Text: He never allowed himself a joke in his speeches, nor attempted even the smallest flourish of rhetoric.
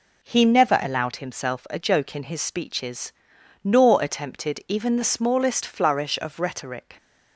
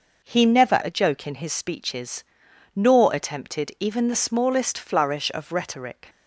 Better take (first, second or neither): first